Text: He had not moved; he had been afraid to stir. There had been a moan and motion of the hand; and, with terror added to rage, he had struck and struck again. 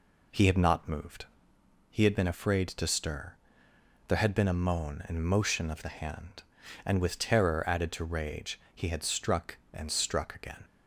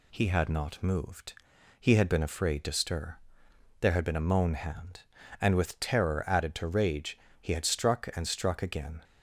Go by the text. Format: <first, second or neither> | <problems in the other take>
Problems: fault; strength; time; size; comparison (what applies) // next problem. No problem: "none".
first | skips "and motion of the"; at 4.5 s